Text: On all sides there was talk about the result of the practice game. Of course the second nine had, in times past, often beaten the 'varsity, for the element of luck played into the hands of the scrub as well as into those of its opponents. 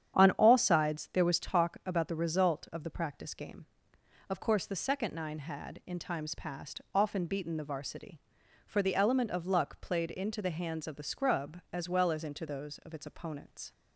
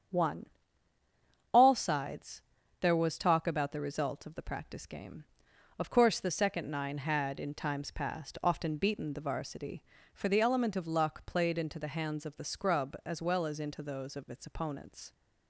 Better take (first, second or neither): first